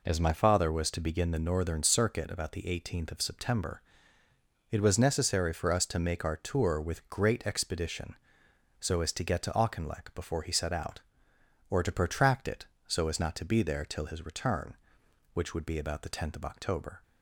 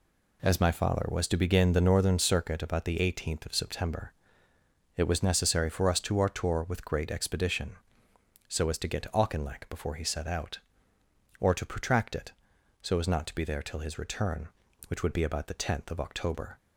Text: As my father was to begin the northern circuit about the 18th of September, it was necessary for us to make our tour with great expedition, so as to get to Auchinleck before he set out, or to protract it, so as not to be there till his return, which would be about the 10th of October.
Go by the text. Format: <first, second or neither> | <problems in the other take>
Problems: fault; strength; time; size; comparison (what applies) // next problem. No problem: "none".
first | skips "make"; at 6.1 s